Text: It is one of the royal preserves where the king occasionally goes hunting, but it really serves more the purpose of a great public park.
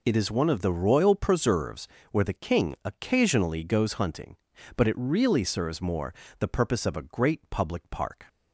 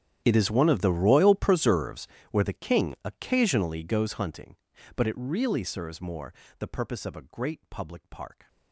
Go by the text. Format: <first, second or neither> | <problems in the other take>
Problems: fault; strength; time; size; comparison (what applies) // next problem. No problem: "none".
first | gets quieter; strong; throughout; 23.5 dB // pauses between "preserves" and "where"; slight; at 2.0 s; 0.24 s long; slight in the first // pauses between "more" and "the"; slight; at 6.3 s; 0.28 s long; slight in the first